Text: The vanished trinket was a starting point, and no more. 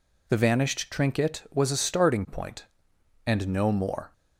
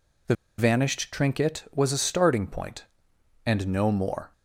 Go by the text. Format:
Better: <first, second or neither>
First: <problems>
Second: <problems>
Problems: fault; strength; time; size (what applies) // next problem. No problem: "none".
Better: first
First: none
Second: pauses between "The" and "vanished"; slight; at 0.3 s; 0.23 s long